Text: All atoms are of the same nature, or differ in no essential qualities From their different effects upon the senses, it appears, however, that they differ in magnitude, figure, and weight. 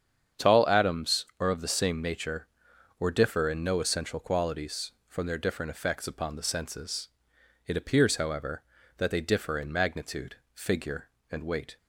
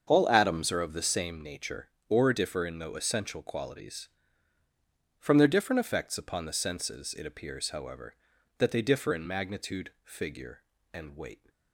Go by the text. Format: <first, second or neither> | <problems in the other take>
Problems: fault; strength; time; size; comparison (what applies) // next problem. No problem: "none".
second | starts louder than the rest; strong; until 1.5 s; 8 dB; also in the second // says "Tall" for "All"; at 0.3 s